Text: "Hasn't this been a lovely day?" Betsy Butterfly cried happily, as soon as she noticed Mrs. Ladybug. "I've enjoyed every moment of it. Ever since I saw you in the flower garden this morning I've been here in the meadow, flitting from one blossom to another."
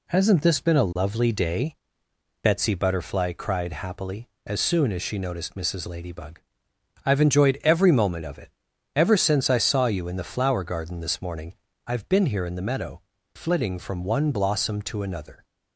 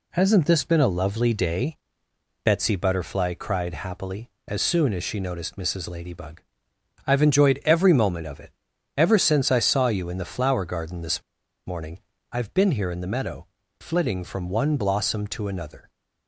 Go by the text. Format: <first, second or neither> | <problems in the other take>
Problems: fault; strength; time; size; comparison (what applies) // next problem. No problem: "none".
first | pauses between "this" and "morning"; at 11.2 s; 0.45 s long // pauses between "morning" and "I've"; slight; at 11.9 s; 0.32 s long; slight in the first